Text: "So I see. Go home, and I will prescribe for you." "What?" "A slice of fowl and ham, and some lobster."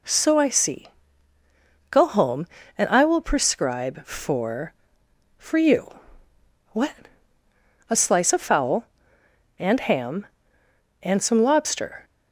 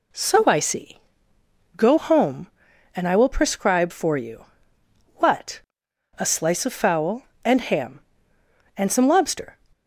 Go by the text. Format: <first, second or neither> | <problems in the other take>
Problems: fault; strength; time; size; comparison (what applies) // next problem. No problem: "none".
second | says "for" twice; at 5.3 s